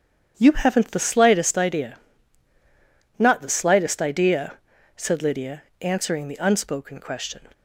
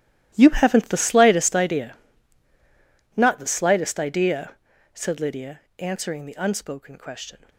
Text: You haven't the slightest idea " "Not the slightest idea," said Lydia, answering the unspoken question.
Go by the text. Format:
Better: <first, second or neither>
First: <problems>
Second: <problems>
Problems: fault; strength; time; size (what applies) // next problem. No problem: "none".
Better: first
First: starts louder than the rest; strong; until 1.3 s; 7.5 dB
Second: gets quieter; strong; throughout; 11 dB // starts louder than the rest; strong; until 1.3 s; 12 dB